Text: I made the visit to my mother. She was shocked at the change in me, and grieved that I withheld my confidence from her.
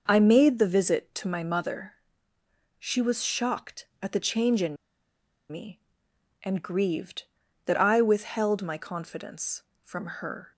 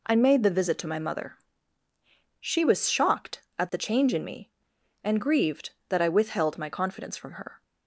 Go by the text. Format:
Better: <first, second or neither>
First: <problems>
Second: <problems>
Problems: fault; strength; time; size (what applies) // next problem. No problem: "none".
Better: second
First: pauses between "in" and "me"; noticeable; at 4.7 s; 0.75 s long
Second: none